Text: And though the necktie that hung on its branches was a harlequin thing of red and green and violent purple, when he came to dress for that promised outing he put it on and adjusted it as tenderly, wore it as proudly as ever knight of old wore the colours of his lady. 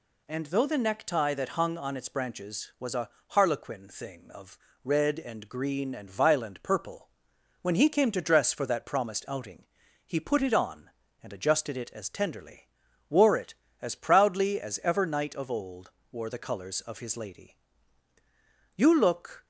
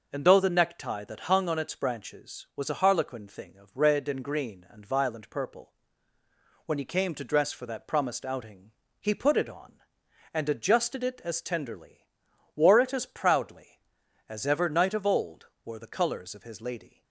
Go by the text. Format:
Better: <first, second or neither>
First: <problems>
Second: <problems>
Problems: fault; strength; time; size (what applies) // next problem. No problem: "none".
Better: second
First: pauses between "a" and "harlequin"; slight; at 3.0 s; 0.20 s long // pauses between "of" and "red"; slight; at 4.5 s; 0.26 s long // pauses between "outing" and "he"; at 9.6 s; 0.40 s long // pauses between "old" and "wore"; slight; at 15.9 s; 0.20 s long // goes on to say "You look"; noticeable; from 18.7 s on; 0.68 s long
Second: pauses between "outing" and "he"; slight; at 8.7 s; 0.30 s long // pauses between "old" and "wore"; slight; at 15.4 s; 0.16 s long